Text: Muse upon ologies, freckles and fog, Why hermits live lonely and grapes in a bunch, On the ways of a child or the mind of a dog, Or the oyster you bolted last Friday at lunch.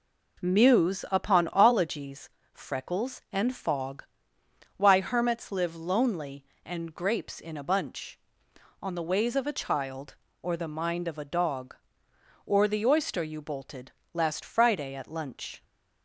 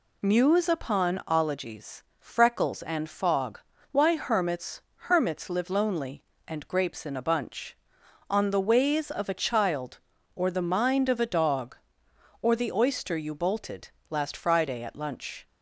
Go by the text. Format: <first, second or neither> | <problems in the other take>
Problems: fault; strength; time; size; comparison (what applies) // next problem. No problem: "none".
first | says "hermits" twice; at 4.9 s // pauses between "bolted" and "last"; slight; at 13.9 s; 0.20 s long; slight in the first